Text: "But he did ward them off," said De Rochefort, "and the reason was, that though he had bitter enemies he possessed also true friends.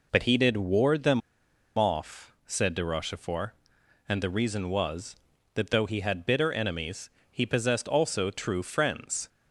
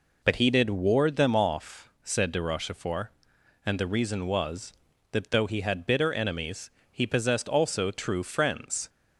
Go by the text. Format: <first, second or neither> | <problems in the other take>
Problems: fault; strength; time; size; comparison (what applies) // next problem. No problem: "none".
second | pauses between "them" and "off"; noticeable; at 1.2 s; 0.57 s long // pauses between "enemies" and "he"; slight; at 7.0 s; 0.22 s long; slight in the second